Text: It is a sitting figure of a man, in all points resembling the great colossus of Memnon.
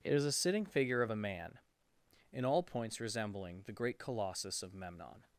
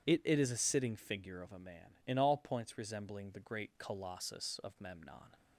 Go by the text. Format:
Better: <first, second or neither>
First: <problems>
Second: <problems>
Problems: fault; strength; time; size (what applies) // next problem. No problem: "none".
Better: first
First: none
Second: starts louder than the rest; strong; until 1.1 s; 9.5 dB // says "It" twice; at 0.2 s